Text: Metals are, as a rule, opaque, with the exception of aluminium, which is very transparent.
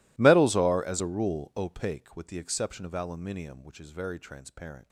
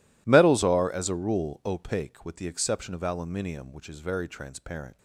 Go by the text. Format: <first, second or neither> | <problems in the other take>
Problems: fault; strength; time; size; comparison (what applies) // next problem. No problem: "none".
second | gets quieter; strong; throughout; 24.5 dB